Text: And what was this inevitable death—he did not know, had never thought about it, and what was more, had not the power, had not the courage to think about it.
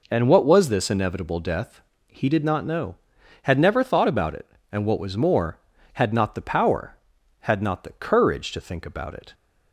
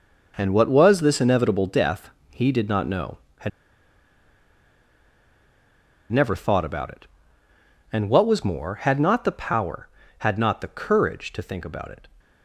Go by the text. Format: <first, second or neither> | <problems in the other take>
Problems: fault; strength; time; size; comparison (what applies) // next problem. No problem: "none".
first | pauses between "had" and "never"; strong; at 3.4 s; 2.6 s long